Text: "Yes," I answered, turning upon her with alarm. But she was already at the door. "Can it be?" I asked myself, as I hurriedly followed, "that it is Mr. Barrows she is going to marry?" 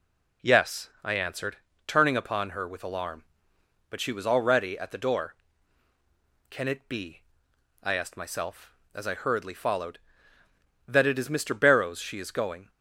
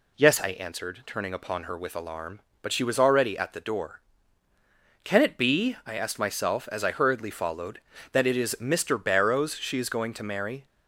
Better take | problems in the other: second | stops before "to marry"; at 12.6 s

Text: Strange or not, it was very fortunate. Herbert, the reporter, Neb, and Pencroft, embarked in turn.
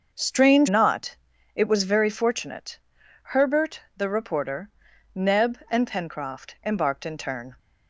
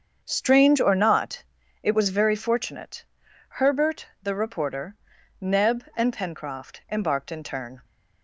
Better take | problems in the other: second | starts louder than the rest; noticeable; until 1.1 s; 6 dB; also in the second // skips "or"; at 0.6 s

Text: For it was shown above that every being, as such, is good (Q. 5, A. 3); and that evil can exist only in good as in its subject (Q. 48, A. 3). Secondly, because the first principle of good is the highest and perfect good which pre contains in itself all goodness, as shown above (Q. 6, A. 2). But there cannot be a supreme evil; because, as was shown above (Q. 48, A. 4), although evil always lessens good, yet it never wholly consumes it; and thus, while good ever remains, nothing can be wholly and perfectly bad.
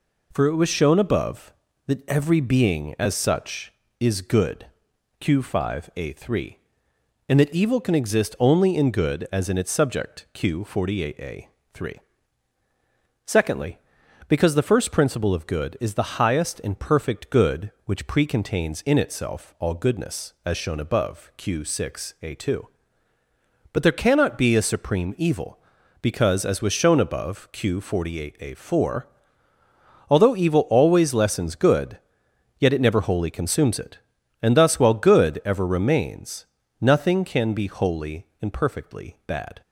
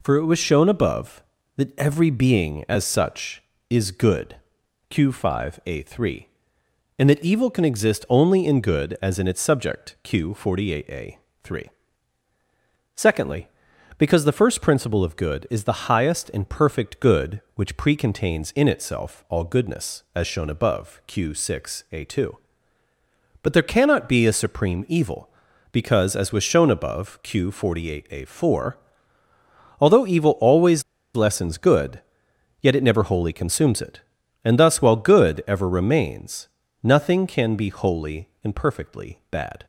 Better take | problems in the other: first | pauses between "always" and "lessens"; slight; at 30.8 s; 0.32 s long

